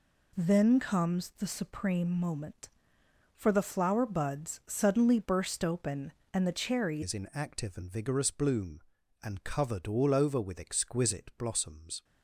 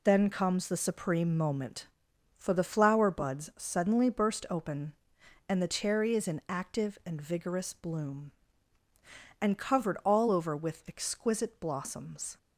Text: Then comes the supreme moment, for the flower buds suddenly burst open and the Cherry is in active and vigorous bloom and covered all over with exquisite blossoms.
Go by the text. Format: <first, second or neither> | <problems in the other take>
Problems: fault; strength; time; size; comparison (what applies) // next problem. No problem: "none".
second | changes voice at "is"; from 7.0 s on; 5.0 s long